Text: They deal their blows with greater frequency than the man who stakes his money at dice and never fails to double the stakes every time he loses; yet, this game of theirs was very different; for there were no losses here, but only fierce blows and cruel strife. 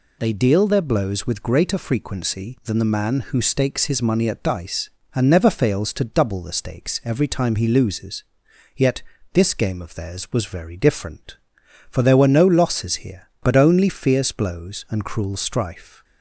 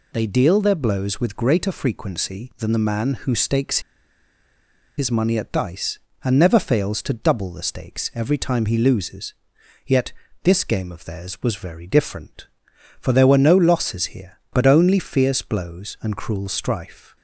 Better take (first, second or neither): first